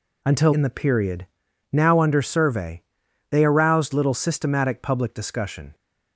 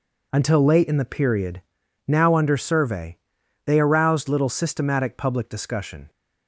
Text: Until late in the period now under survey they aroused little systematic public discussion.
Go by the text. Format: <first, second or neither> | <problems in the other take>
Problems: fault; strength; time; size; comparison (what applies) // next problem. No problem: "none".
second | skips "late"; at 0.5 s // pauses between "period" and "now"; at 1.2 s; 0.44 s long; also in the second // pauses between "survey" and "they"; noticeable; at 2.8 s; 0.48 s long; noticeable in the second